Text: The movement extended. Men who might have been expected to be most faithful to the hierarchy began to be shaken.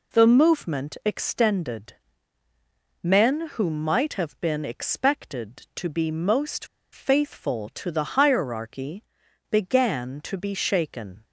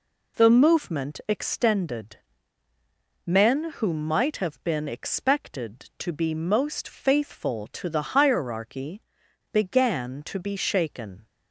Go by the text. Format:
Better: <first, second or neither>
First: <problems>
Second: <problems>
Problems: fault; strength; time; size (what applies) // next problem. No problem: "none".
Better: second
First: pauses between "most" and "faithful"; slight; at 6.6 s; 0.27 s long // pauses between "hierarchy" and "began"; noticeable; at 9.0 s; 0.48 s long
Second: pauses between "hierarchy" and "began"; noticeable; at 9.0 s; 0.51 s long